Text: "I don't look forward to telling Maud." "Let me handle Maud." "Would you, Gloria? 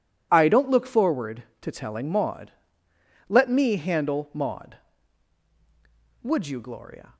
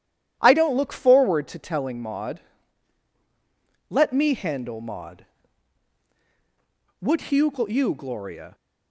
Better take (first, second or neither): first